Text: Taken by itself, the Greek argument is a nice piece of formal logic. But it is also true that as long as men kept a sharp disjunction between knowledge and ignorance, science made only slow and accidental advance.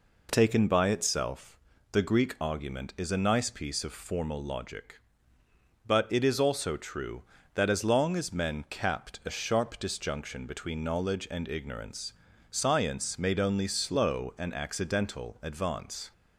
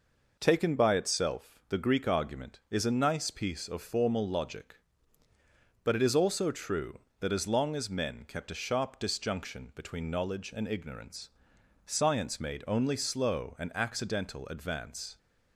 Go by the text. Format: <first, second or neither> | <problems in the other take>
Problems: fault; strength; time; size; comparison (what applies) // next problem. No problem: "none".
second | says "capped" for "kept"; at 8.6 s